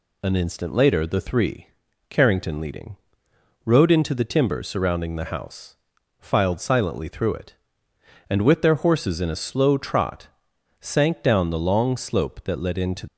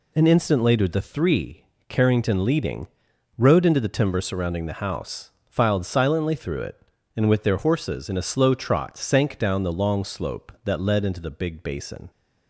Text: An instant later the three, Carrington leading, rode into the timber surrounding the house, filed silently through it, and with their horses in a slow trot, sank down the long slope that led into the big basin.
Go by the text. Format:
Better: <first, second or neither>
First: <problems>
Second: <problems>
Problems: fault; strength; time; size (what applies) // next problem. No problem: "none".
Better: second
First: stops before "the big basin"; at 13.0 s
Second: none